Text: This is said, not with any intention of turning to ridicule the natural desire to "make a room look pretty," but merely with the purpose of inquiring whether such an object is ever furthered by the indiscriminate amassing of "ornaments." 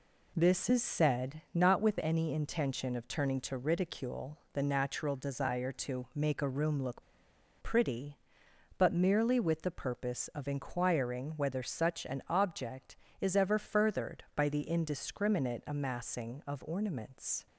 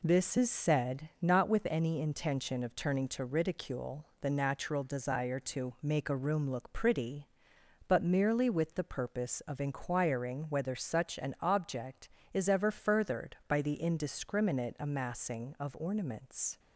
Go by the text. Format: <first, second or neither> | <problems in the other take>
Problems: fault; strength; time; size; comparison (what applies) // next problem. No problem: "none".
second | pauses between "ridicule" and "the"; slight; at 4.3 s; 0.16 s long; slight in the second // pauses between "look" and "pretty"; noticeable; at 7.0 s; 0.59 s long